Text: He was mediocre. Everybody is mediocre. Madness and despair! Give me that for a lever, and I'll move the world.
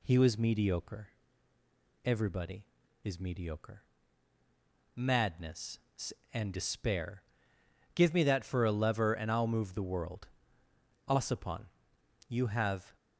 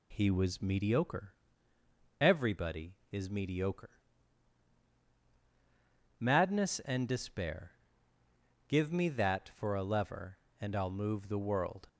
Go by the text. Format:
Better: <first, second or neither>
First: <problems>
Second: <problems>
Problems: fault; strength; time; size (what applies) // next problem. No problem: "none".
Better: second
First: goes on to say "Ossipon you have"; strong; from 11.0 s on; 1.8 s long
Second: none